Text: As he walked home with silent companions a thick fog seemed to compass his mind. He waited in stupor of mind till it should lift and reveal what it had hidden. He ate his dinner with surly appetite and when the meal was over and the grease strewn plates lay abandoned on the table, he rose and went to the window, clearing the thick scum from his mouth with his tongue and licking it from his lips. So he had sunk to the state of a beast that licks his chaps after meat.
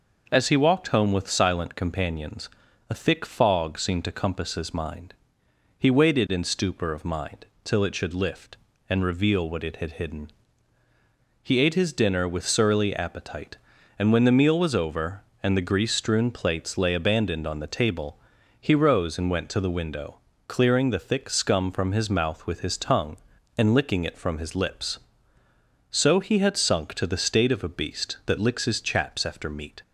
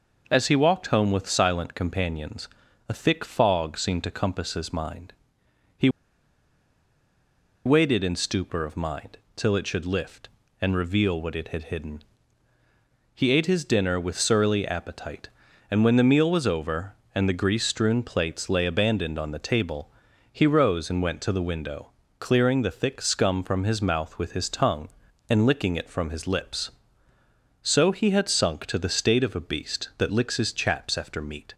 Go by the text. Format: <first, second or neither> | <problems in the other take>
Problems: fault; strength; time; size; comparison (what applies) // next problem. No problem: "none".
first | pauses between "companions" and "a"; at 2.4 s; 0.40 s long; also in the first // pauses between "He" and "waited"; strong; at 5.8 s; 1.7 s long // pauses between "mind" and "till"; slight; at 9.1 s; 0.16 s long; slight in the first